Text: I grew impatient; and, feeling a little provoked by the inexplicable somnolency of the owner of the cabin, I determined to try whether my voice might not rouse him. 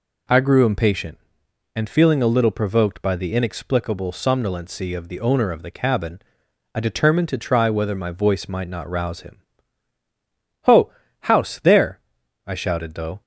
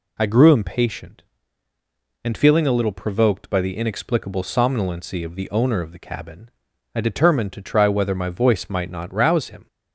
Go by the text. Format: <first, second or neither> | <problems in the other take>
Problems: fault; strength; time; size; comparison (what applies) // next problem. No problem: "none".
second | goes on to say "Ho house there I shouted though"; strong; from 10.6 s on; 2.5 s long